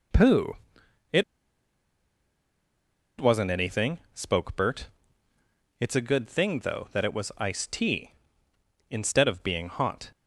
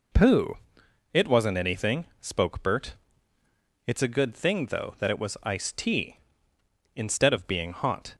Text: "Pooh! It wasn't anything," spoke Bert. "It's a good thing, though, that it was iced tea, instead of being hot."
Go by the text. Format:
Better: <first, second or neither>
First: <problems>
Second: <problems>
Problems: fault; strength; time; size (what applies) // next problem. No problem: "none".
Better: second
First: pauses between "It" and "wasn't"; strong; at 1.2 s; 1.9 s long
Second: none